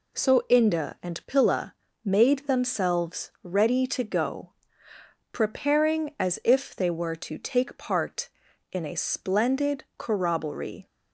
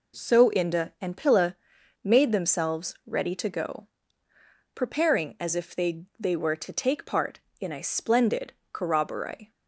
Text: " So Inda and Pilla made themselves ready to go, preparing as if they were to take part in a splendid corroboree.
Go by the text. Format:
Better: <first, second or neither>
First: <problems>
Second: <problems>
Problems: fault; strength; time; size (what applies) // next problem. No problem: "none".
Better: first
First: pauses between "Pilla" and "made"; slight; at 1.7 s; 0.30 s long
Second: pauses between "Pilla" and "made"; noticeable; at 1.5 s; 0.48 s long // says "they" twice; at 6.1 s // pauses between "splendid" and "corroboree"; slight; at 8.5 s; 0.18 s long